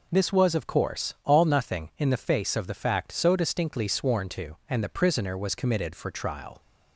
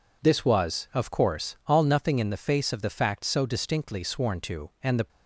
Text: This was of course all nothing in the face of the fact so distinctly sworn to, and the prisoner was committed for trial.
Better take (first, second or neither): first